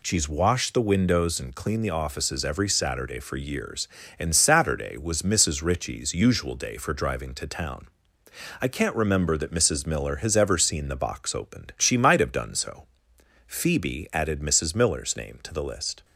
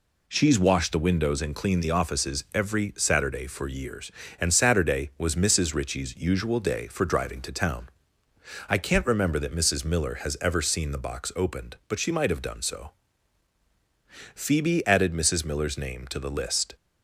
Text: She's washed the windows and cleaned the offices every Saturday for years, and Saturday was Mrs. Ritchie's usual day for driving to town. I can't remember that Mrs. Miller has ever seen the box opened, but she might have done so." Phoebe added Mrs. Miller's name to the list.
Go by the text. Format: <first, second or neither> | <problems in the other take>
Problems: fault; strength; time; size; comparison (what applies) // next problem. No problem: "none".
second | skips "but"; at 11.7 s